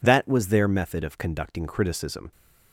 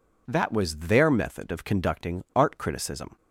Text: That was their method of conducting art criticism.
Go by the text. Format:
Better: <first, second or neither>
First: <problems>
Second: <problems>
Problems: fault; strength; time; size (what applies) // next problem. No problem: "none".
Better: second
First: skips "art"; at 1.6 s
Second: none